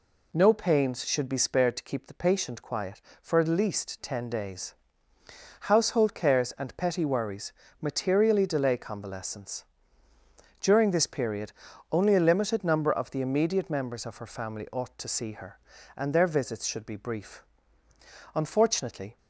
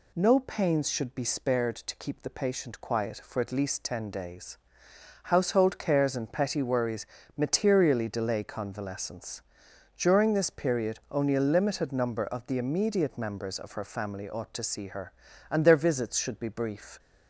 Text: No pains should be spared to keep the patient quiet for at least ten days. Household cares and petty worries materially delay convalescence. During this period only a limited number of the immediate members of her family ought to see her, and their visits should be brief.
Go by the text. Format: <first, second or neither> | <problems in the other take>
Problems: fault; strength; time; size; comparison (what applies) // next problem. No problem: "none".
second | pauses between "worries" and "materially"; slight; at 7.5 s; 0.30 s long; slight in the second // pauses between "period" and "only"; at 11.5 s; 0.40 s long // goes on to say "Unfortunately"; noticeable; from 18.3 s on; 0.82 s long